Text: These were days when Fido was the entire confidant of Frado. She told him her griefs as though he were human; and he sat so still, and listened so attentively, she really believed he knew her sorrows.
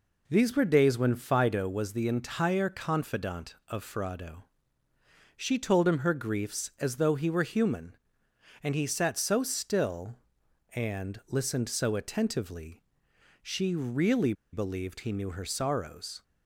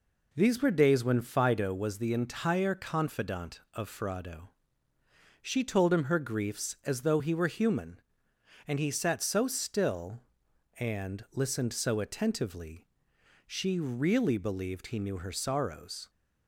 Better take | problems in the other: second | pauses between "really" and "believed"; slight; at 14.3 s; 0.19 s long

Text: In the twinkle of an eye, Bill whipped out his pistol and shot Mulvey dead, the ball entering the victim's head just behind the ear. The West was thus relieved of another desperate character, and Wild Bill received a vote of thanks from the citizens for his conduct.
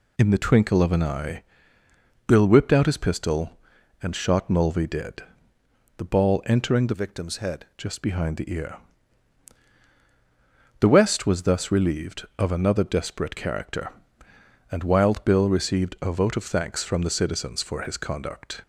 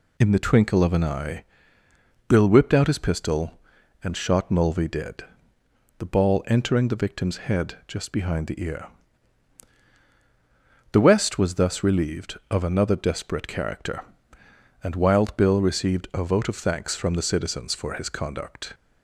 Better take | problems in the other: second | changes voice from "victim's" to "head"; from 6.9 to 7.6 s; 0.7 s long

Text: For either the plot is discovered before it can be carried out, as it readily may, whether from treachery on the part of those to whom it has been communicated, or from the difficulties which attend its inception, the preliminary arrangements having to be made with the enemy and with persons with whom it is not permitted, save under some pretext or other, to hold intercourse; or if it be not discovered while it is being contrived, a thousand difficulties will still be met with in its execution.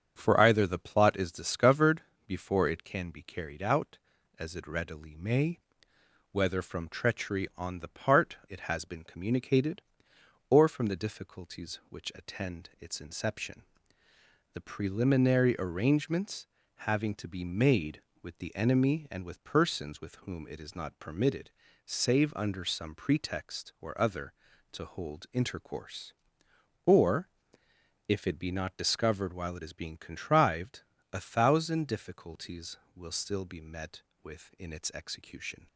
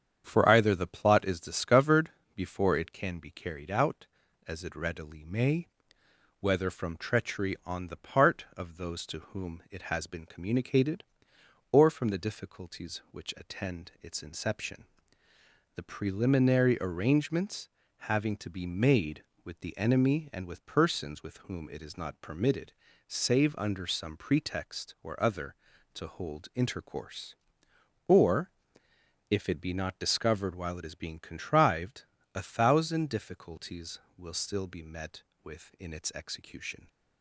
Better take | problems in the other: second | starts louder than the rest; strong; until 1.1 s; 7.5 dB; strong in the second // pauses between "discovered" and "before"; slight; at 2.0 s; 0.26 s long; slight in the second // skips "of those to whom"; at 8.4 s // pauses between "arrangements" and "having"; at 16.4 s; 0.42 s long; also in the second // pauses between "or" and "if"; noticeable; at 27.2 s; 0.78 s long; noticeable in the second

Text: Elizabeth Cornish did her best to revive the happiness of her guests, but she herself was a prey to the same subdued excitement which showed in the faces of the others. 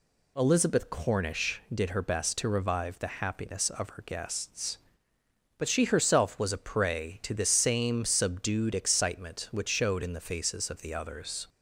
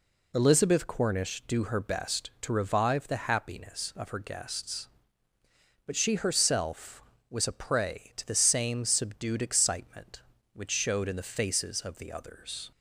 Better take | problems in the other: first | says "do" for "did"; at 1.4 s

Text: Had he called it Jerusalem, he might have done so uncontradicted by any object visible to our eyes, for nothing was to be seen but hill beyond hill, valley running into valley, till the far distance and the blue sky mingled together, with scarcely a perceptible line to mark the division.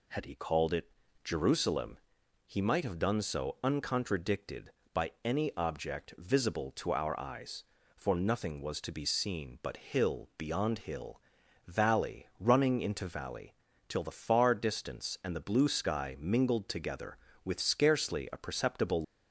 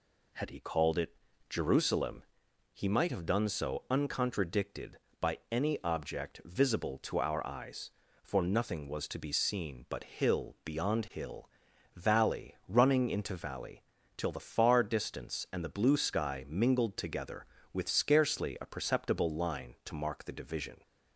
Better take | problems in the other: second | pauses between "it" and "Jerusalem"; slight; at 0.8 s; 0.33 s long; slight in the second // stops before "line to mark the division"; at 19.0 s

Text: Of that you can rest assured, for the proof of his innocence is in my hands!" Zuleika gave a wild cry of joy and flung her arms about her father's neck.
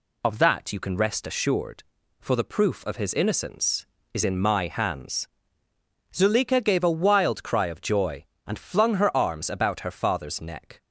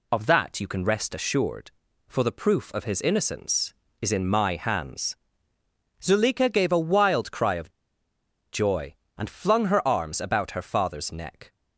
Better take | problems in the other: first | pauses between "of" and "joy"; noticeable; at 7.6 s; 0.84 s long

